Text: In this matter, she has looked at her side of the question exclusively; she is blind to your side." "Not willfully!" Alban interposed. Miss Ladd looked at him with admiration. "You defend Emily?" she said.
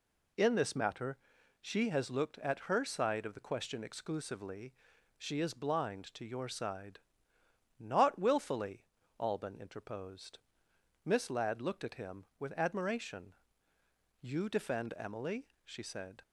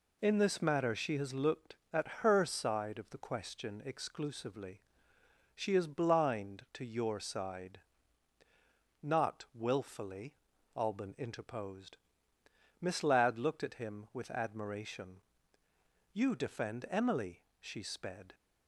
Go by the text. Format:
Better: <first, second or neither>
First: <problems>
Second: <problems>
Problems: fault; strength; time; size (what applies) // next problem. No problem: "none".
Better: first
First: none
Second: says "sped" for "said"; at 17.8 s